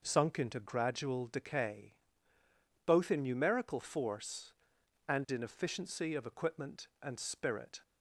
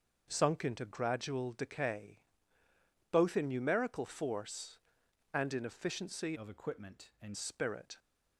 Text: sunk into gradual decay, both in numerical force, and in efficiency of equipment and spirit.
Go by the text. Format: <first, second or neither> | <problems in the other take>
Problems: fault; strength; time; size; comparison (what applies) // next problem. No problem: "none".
first | changes voice from "of" to "and"; from 6.3 to 7.3 s; 1.0 s long